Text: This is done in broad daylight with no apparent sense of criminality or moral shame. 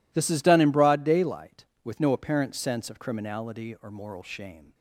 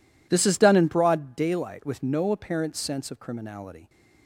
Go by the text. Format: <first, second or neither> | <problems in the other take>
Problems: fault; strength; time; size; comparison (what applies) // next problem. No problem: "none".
first | stops before "or moral shame"; at 3.8 s